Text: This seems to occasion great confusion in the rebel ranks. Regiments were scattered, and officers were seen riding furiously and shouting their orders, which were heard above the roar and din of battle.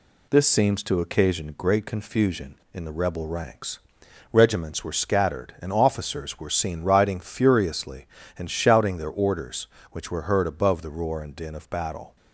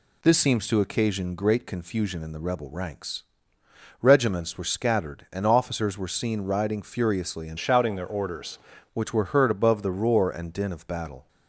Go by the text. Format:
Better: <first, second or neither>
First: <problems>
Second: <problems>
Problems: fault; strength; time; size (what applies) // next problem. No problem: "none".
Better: first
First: none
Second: changes voice from "shouting" to "orders"; from 7.5 to 8.5 s; 1.0 s long